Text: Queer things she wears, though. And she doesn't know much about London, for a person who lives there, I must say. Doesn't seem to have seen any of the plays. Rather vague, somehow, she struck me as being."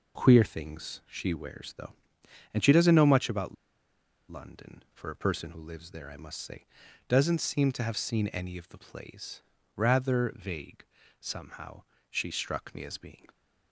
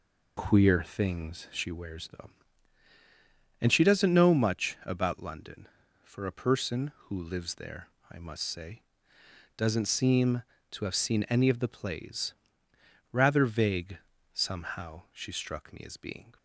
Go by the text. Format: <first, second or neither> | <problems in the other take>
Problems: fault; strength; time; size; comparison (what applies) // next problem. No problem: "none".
second | pauses between "about" and "London"; noticeable; at 3.5 s; 0.74 s long